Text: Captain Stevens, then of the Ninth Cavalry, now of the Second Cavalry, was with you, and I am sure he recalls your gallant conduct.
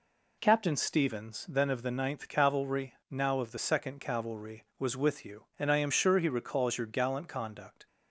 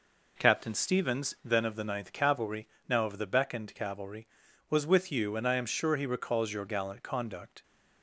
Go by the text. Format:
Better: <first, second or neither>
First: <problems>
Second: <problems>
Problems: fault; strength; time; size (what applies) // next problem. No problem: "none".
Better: first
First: none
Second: says "Beckoned" for "Second"; at 3.2 s